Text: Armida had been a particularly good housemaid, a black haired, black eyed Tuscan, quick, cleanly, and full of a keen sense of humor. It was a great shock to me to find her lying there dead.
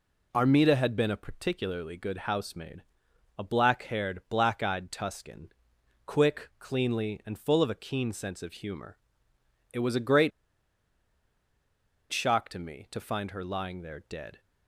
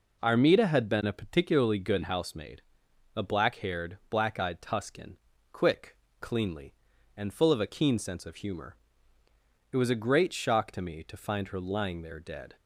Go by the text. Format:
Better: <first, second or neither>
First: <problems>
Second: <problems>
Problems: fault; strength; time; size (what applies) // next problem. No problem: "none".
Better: second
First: pauses between "great" and "shock"; strong; at 10.3 s; 1.8 s long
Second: none